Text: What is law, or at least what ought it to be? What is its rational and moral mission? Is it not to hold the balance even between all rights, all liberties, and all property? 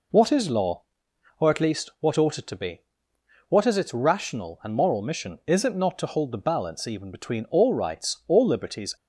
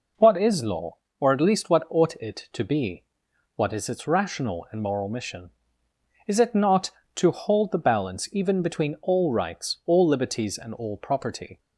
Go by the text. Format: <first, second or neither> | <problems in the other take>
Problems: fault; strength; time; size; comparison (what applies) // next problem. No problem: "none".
second | stops before "and all property"; at 8.9 s